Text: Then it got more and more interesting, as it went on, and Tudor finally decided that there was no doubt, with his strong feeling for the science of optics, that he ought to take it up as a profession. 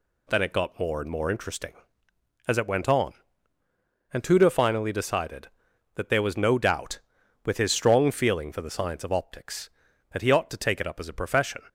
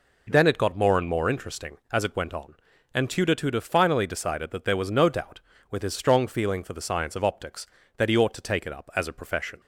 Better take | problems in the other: first | says "Tudor" twice; at 3.3 s

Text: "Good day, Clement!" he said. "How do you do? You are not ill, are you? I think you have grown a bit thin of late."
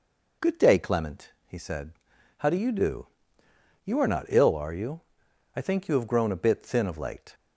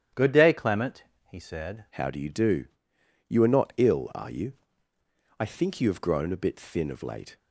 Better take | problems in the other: first | starts louder than the rest; strong; until 1.4 s; 10 dB // changes voice at "How"; from 1.9 s on; 5.4 s long

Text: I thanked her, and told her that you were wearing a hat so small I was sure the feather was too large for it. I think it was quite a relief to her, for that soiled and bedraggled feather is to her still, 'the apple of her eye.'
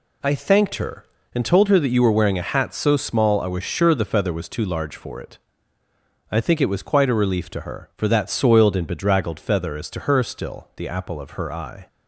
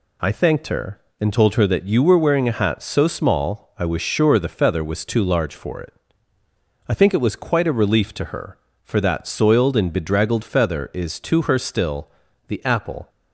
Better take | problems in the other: first | stops before "of her eye"; at 13.0 s

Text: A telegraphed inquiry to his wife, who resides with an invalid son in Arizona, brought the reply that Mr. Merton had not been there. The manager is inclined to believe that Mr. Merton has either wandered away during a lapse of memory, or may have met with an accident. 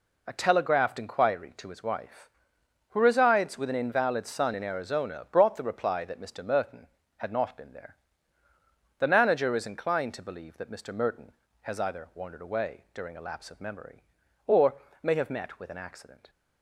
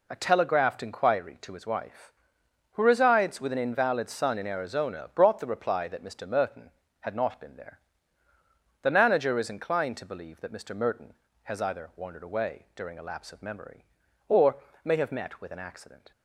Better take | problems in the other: neither | pauses between "or" and "may"; slight; the same in both

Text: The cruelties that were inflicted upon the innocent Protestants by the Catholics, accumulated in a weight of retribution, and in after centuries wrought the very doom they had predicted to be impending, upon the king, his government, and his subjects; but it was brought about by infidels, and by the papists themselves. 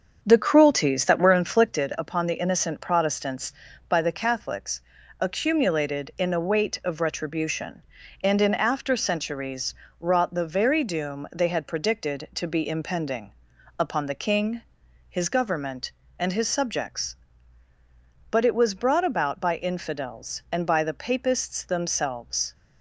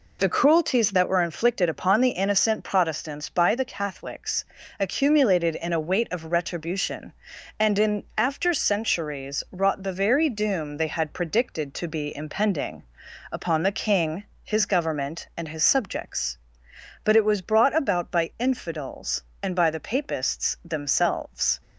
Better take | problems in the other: second | starts louder than the rest; until 2.0 s; 6.5 dB // pauses between "centuries" and "wrought"; slight; at 9.7 s; 0.26 s long

